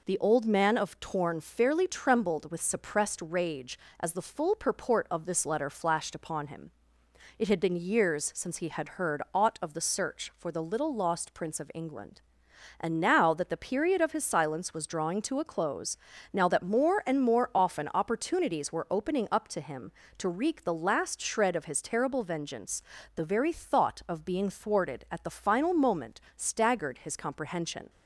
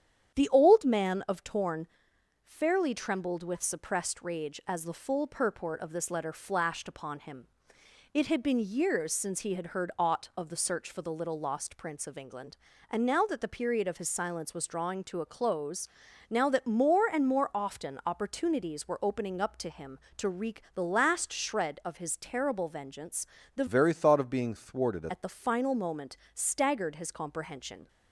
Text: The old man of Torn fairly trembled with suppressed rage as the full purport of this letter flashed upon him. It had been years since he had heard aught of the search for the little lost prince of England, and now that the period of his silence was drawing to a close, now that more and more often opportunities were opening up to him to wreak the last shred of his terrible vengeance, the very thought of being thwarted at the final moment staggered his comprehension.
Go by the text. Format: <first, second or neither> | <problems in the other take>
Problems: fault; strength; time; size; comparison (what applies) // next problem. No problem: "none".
first | starts louder than the rest; strong; until 1.3 s; 9 dB // pauses between "Torn" and "fairly"; noticeable; at 1.8 s; 0.56 s long // changes voice from "very" to "thwarted"; from 23.6 to 25.0 s; 1.4 s long // pauses between "moment" and "staggered"; slight; at 26.1 s; 0.18 s long; slight in the first